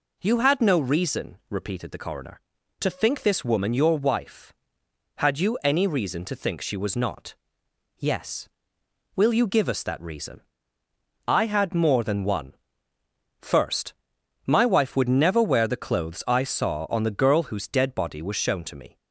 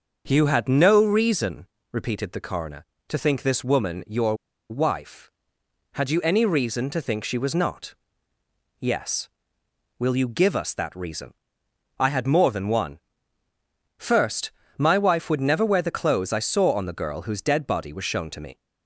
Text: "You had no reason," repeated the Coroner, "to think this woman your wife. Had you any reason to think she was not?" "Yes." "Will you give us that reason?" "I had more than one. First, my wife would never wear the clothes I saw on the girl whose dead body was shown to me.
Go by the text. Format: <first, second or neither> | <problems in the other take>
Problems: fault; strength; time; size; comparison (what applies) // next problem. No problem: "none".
first | starts louder than the rest; until 1.2 s; 6 dB // pauses between "your" and "wife"; slight; at 4.3 s; 0.35 s long